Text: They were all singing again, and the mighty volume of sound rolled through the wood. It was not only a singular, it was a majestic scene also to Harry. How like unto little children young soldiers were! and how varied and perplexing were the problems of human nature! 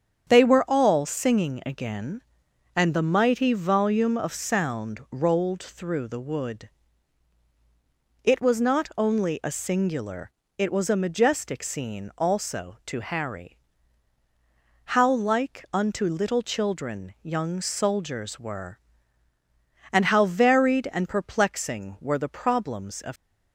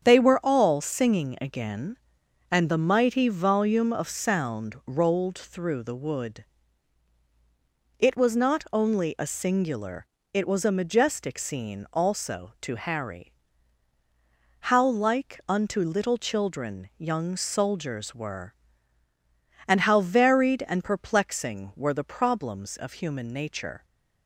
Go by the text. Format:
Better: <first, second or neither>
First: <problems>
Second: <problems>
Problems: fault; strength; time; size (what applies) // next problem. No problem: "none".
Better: second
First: starts louder than the rest; strong; until 1.3 s; 8 dB // stops before "human nature"; at 23.1 s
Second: starts louder than the rest; strong; until 1.0 s; 8 dB